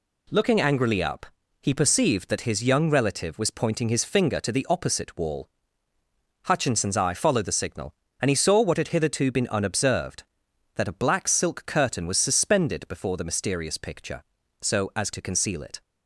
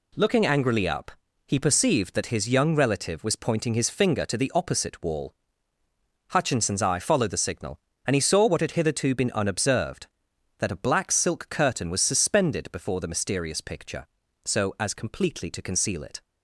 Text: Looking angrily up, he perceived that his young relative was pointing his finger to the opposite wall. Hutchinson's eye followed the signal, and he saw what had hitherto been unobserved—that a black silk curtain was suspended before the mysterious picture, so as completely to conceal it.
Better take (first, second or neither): second